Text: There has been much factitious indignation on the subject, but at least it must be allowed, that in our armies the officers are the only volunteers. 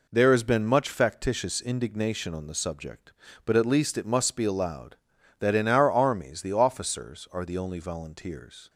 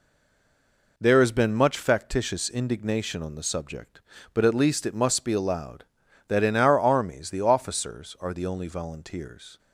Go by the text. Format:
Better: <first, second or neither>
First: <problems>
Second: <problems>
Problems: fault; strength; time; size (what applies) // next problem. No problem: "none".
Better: first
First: none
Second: stays silent before the first word; until 0.9 s; 0.9 s long